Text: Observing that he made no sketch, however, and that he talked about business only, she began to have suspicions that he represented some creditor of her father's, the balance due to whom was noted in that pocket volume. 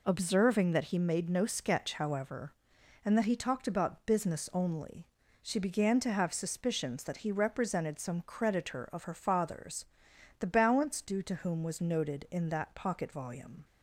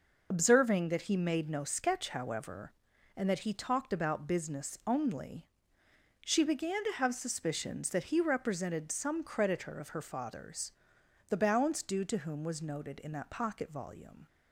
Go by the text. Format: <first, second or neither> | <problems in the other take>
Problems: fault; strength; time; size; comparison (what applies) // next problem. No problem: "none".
first | loses the start of "Observing"; at 0.3 s; 40 ms